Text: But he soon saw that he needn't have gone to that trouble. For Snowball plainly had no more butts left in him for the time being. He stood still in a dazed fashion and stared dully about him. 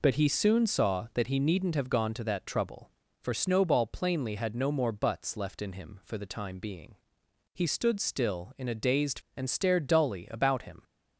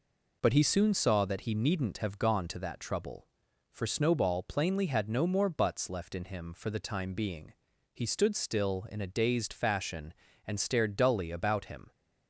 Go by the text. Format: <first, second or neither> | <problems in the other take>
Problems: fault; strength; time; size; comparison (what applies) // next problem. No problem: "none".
second | skips "fashion"; at 9.2 s